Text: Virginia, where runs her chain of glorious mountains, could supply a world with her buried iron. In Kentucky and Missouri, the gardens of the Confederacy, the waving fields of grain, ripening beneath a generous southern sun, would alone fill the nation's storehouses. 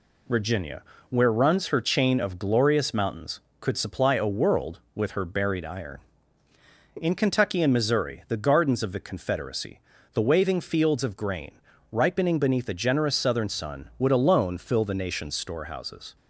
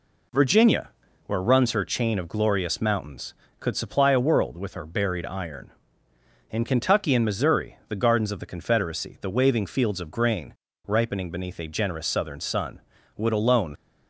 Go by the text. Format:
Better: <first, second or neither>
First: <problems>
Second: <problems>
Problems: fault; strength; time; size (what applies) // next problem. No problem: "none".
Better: first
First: none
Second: stops before "fill the nation's storehouses"; at 13.7 s